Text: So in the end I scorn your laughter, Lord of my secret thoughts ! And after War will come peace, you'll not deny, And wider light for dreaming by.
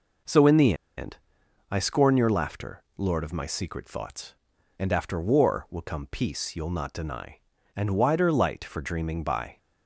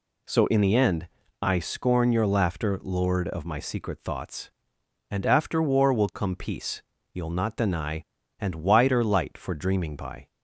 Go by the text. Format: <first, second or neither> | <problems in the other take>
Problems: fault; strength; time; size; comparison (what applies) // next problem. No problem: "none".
second | pauses between "the" and "end"; slight; at 0.7 s; 0.22 s long // pauses between "end" and "I"; noticeable; at 1.1 s; 0.52 s long; slight in the second